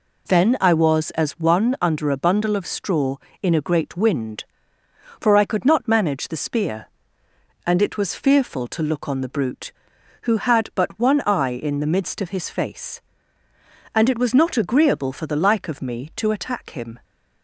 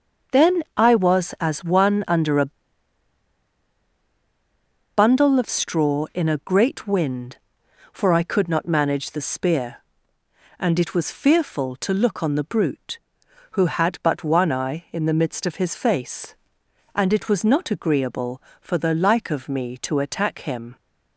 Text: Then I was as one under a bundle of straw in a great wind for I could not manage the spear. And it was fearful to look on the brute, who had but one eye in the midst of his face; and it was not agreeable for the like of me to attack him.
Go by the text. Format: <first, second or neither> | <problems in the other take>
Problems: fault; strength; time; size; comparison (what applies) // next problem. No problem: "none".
first | starts louder than the rest; until 1.5 s; 6.5 dB // pauses between "a" and "bundle"; strong; at 2.5 s; 2.4 s long